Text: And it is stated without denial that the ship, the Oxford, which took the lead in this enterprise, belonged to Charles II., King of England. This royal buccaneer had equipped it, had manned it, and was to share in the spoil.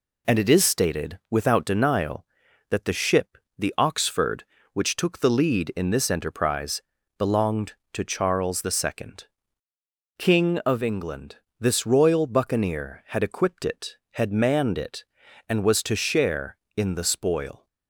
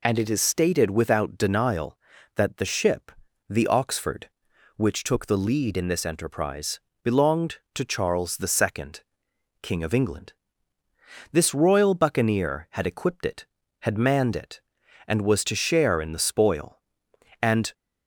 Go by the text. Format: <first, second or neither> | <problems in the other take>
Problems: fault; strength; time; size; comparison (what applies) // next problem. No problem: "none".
first | goes on to say "And"; slight; from 17.4 s on; 0.32 s long